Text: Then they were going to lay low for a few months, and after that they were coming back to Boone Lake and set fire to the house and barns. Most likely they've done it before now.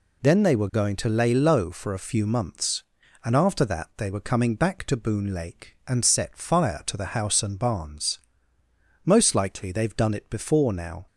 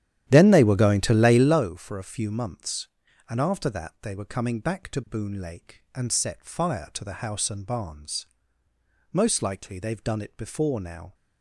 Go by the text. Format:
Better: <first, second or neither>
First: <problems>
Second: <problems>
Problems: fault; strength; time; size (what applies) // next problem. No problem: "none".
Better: first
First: none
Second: starts louder than the rest; strong; until 1.6 s; 11.5 dB